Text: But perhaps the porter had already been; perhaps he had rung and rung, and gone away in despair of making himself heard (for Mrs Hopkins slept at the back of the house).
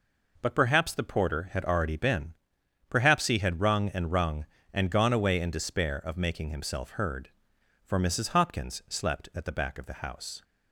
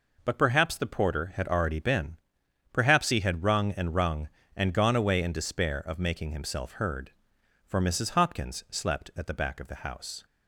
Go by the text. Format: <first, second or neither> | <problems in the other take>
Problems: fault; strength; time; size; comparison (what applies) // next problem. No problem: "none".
neither | none